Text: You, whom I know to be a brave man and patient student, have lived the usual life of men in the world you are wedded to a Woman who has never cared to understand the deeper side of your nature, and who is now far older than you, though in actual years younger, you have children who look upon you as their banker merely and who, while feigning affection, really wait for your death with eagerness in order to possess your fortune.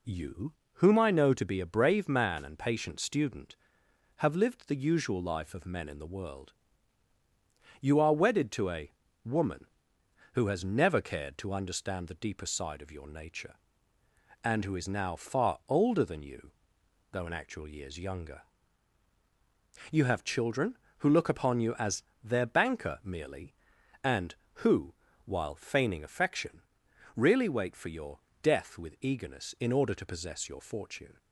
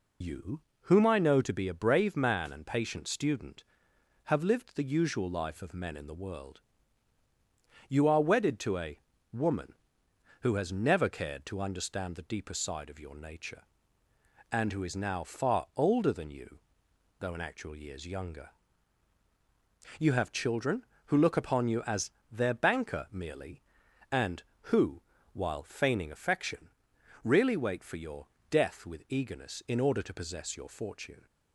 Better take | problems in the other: first | loses the start of "You"; at 0.2 s; 60 ms // pauses between "world" and "you"; strong; at 6.6 s; 1.2 s long; strong in the first // pauses between "a" and "Woman"; slight; at 8.9 s; 0.34 s long; slight in the first // pauses between "as" and "their"; slight; at 22.1 s; 0.18 s long; slight in the first // pauses between "your" and "death"; slight; at 28.2 s; 0.24 s long; slight in the first

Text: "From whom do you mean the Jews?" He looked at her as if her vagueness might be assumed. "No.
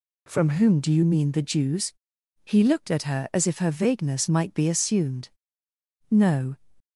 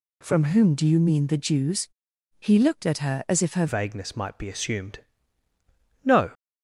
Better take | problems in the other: first | changes voice at "vagueness"; from 3.6 s on; 2.7 s long

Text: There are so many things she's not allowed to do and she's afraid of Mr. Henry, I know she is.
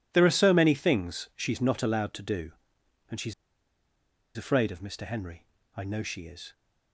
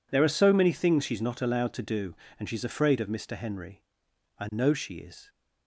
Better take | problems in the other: second | pauses between "she's" and "afraid"; at 3.3 s; 1.0 s long

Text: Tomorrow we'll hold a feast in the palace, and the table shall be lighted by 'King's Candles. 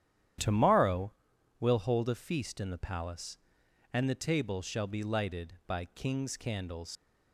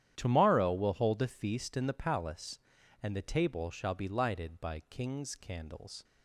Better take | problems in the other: second | starts louder than the rest; strong; until 1.8 s; 10.5 dB; strong in the second // pauses between "Tomorrow" and "we'll"; noticeable; at 1.1 s; 0.48 s long // leaves "Candles" unfinished; at 6.9 s; 120 ms

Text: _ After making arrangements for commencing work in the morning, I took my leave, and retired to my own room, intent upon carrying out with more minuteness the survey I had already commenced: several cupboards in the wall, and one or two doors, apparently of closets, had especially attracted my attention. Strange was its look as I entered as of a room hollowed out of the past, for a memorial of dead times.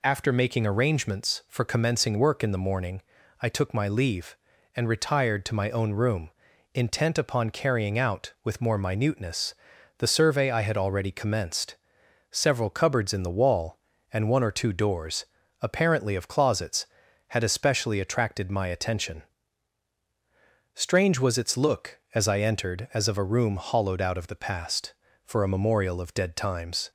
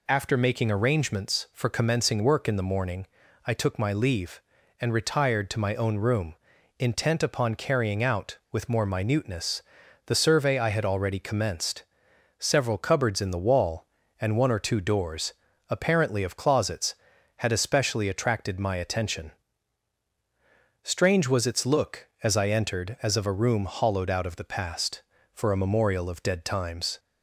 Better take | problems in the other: neither | pauses between "minuteness" and "the"; noticeable; the same in both

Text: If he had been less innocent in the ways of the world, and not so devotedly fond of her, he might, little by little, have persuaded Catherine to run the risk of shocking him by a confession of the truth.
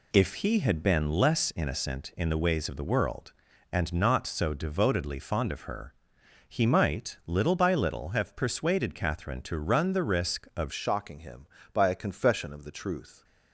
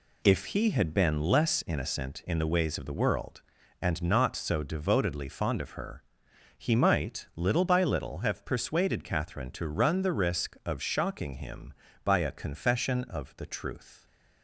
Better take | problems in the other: second | changes voice at "shocking"; from 10.7 s on; 2.5 s long

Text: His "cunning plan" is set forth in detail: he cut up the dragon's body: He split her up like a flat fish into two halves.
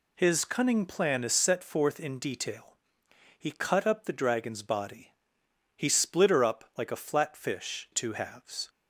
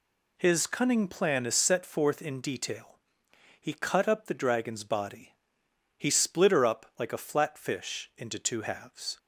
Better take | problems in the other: second | skips "into"; at 7.8 s

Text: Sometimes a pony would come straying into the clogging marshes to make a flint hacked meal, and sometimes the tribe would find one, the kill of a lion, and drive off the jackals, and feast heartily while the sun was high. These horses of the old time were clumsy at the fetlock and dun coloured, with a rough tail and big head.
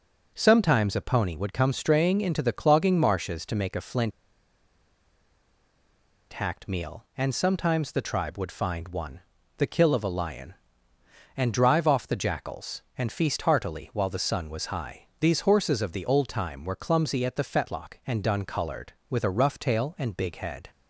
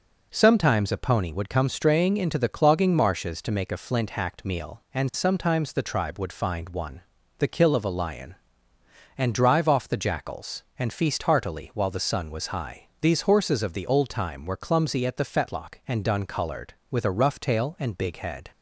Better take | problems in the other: second | pauses between "flint" and "hacked"; strong; at 4.1 s; 2.2 s long

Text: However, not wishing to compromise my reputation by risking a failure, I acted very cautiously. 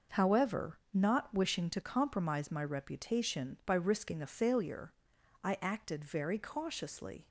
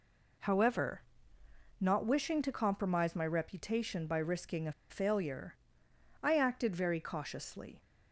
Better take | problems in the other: first | pauses between "a" and "failure"; slight; at 4.7 s; 0.17 s long

